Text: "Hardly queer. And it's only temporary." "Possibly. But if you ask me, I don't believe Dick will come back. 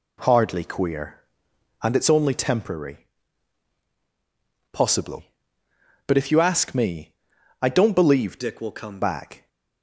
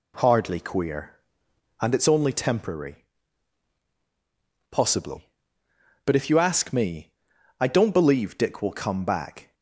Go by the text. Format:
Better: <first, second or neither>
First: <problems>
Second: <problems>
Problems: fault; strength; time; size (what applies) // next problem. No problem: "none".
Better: second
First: changes voice from "Dick" to "come"; from 8.3 to 9.0 s; 0.7 s long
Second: none